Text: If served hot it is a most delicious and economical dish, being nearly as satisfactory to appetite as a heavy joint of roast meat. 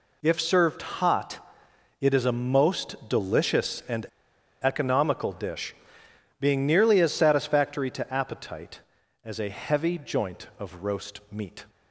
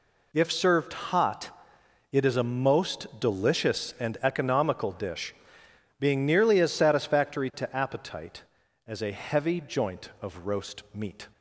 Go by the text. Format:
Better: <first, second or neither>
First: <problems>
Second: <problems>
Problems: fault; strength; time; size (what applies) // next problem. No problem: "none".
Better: second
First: pauses between "hot" and "it"; noticeable; at 1.3 s; 0.62 s long // pauses between "and" and "economical"; noticeable; at 4.0 s; 0.57 s long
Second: pauses between "hot" and "it"; noticeable; at 1.4 s; 0.62 s long